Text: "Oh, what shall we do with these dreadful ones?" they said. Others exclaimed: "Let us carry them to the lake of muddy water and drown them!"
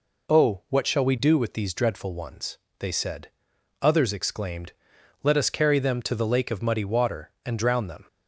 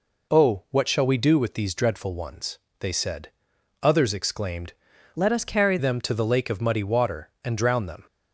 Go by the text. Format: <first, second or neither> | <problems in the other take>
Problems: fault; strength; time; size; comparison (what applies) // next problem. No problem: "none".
first | changes voice from "Let" to "carry"; from 5.1 to 5.7 s; 0.6 s long